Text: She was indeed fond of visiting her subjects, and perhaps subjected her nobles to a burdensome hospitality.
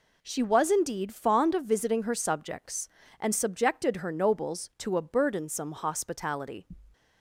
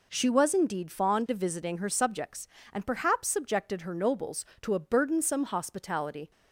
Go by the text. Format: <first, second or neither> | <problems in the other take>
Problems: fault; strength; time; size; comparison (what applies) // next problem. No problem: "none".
second | skips "perhaps"; at 3.3 s